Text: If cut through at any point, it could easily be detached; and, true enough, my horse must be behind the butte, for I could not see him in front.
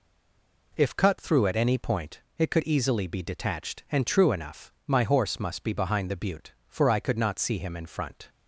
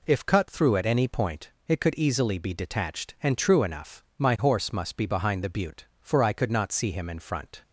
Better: second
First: stays silent before the first word; slight; until 0.7 s; 0.7 s long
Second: none

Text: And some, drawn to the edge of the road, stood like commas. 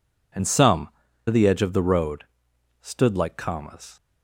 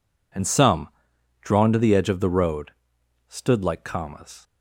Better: second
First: skips "drawn"; at 1.0 s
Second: none

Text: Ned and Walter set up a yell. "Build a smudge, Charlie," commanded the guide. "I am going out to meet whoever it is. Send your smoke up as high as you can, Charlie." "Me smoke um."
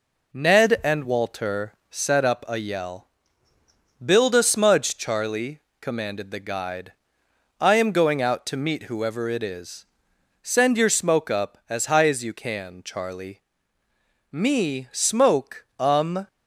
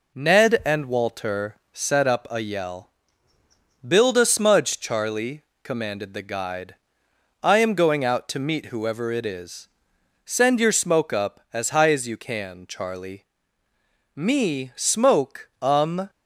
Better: neither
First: none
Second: none

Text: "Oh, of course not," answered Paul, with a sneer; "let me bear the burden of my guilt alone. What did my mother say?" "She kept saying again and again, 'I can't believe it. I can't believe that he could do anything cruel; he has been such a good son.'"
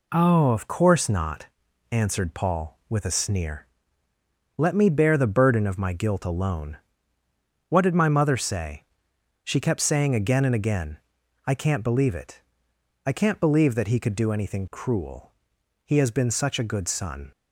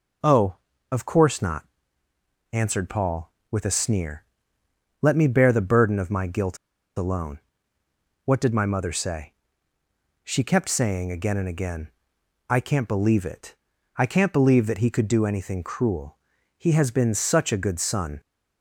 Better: first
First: none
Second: pauses between "guilt" and "alone"; at 6.5 s; 0.40 s long

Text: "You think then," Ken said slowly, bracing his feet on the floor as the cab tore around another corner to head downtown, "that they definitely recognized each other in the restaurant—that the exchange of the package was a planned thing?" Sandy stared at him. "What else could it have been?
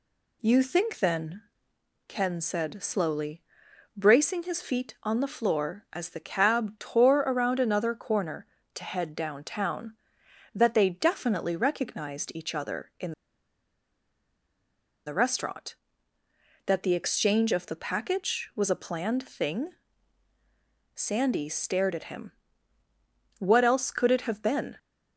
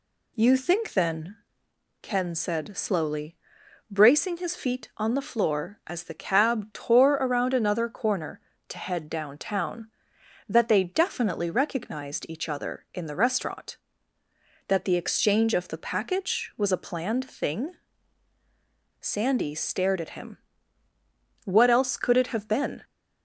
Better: second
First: pauses between "in" and "the"; strong; at 13.1 s; 1.9 s long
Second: none

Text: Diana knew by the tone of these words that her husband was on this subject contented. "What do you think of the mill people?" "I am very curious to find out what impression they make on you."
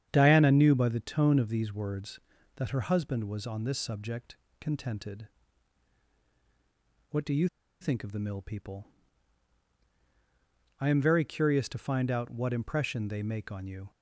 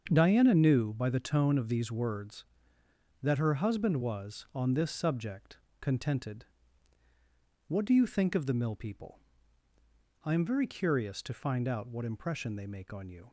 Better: second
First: starts louder than the rest; strong; until 1.1 s; 8.5 dB // pauses between "subject" and "contented"; slight; at 4.3 s; 0.22 s long // pauses between "you" and "think"; slight; at 7.4 s; 0.34 s long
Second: starts louder than the rest; until 1.1 s; 7 dB // pauses between "subject" and "contented"; slight; at 5.5 s; 0.22 s long

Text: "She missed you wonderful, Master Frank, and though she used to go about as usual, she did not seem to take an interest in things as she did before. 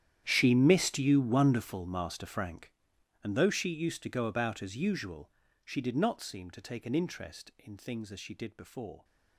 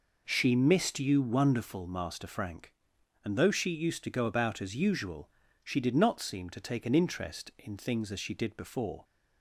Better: second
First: gets quieter; strong; throughout; 18.5 dB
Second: none

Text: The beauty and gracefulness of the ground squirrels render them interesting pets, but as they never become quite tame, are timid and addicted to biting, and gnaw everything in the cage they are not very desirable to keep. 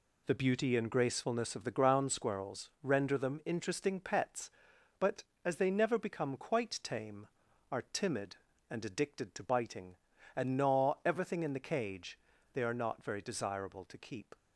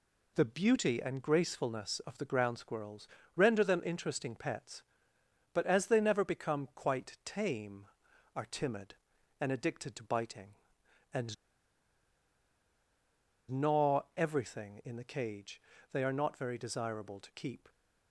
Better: first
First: pauses between "cage" and "they"; slight; at 12.1 s; 0.34 s long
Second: pauses between "squirrels" and "render"; slight; at 3.0 s; 0.28 s long // pauses between "and" and "gnaw"; strong; at 11.3 s; 2.1 s long // pauses between "cage" and "they"; slight; at 15.6 s; 0.30 s long

